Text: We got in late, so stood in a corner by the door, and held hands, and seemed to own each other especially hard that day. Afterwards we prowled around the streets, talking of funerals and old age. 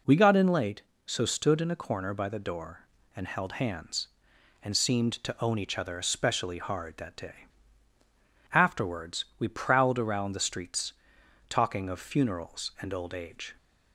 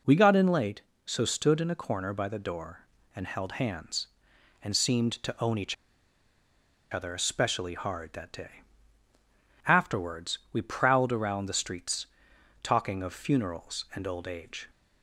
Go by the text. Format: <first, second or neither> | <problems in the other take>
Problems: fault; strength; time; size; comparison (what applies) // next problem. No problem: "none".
first | pauses between "each" and "other"; at 5.7 s; 1.1 s long // pauses between "Afterwards" and "we"; slight; at 10.3 s; 0.16 s long; slight in the first